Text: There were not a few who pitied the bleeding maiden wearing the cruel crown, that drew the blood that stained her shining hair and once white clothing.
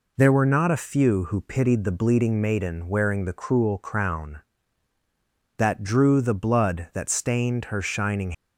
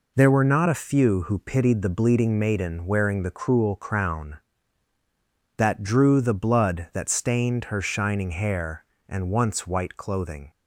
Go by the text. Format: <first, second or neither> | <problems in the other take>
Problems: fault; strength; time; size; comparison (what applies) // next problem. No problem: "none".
second | stops before "hair and once white clothing"; at 8.3 s